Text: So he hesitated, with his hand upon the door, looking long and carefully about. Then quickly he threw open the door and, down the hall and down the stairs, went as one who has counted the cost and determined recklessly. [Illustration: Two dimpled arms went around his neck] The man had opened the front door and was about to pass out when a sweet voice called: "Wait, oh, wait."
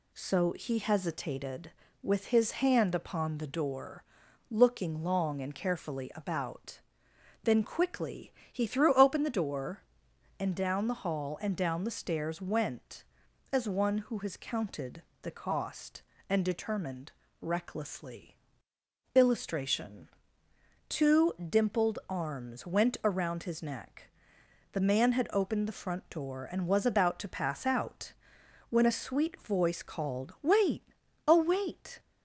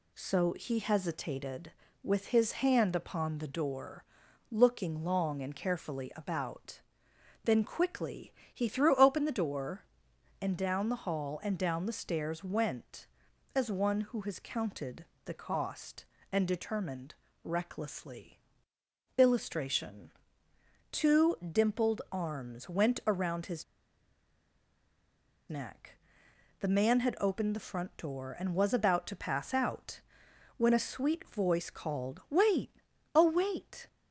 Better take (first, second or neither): first